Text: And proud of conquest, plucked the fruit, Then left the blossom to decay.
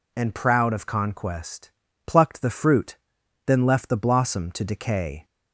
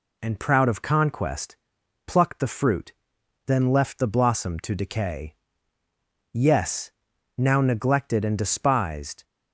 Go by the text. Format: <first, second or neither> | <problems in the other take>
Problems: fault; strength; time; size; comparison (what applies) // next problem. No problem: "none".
first | goes on to say "Yes now neglected and despised"; strong; from 6.3 s on; 2.9 s long